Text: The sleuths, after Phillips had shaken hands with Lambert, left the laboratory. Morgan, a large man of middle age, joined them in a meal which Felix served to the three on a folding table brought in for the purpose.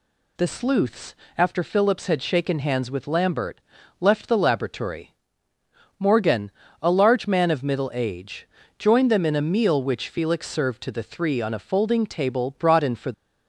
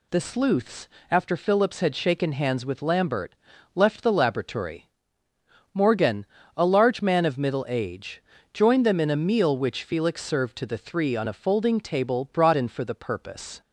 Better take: second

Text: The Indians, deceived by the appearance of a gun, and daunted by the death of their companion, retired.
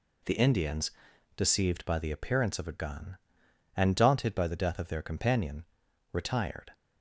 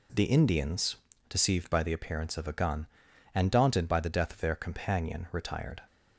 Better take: neither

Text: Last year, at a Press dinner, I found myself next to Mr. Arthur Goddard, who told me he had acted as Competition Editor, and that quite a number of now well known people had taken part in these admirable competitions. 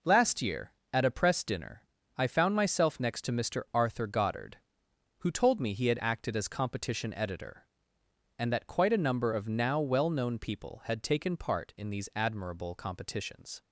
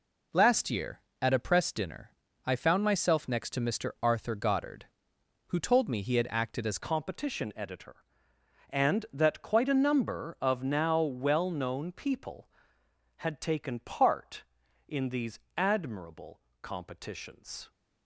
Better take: first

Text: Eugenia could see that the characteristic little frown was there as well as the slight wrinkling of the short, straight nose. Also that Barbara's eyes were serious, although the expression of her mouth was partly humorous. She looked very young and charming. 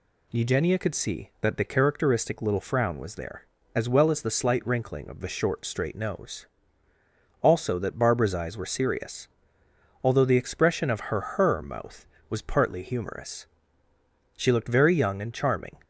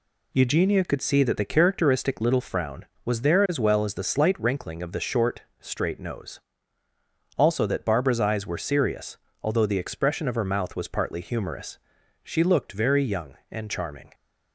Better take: second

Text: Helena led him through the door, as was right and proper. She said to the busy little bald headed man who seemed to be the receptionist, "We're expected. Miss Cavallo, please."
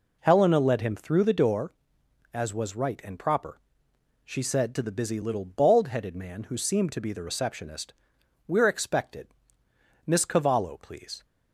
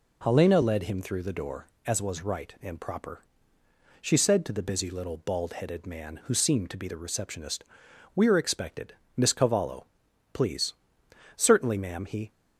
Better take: first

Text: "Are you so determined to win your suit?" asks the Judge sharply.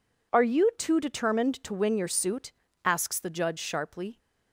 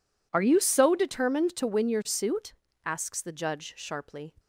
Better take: second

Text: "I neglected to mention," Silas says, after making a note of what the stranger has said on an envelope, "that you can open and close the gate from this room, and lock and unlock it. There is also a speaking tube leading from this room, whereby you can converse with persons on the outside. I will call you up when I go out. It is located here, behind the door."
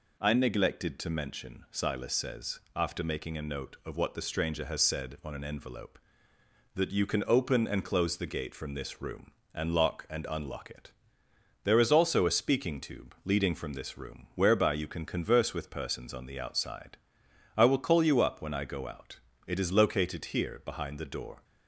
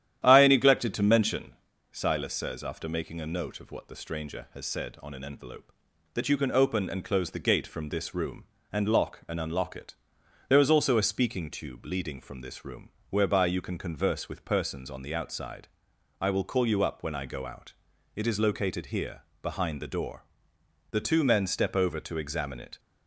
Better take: first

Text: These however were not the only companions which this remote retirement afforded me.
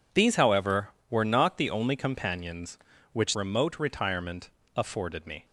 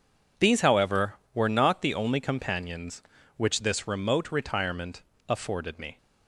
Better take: second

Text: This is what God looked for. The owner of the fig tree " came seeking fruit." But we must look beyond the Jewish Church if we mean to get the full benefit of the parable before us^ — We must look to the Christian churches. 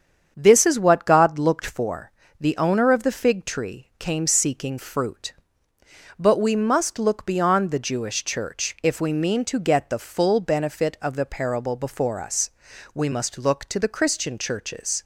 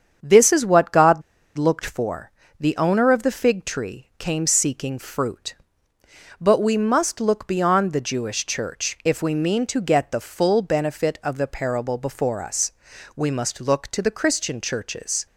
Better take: first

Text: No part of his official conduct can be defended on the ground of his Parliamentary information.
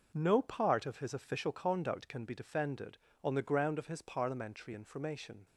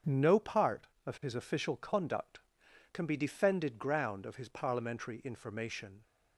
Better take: first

